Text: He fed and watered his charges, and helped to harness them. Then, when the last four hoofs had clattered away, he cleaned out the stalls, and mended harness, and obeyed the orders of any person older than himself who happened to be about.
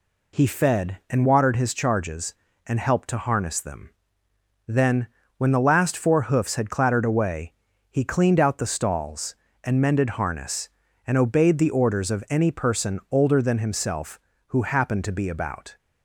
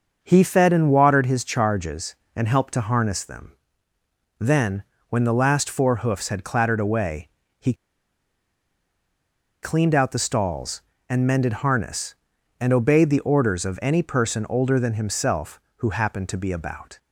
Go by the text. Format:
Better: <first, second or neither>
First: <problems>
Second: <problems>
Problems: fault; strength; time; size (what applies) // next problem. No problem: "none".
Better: first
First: none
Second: starts louder than the rest; until 1.2 s; 6.5 dB // pauses between "he" and "cleaned"; strong; at 7.7 s; 1.8 s long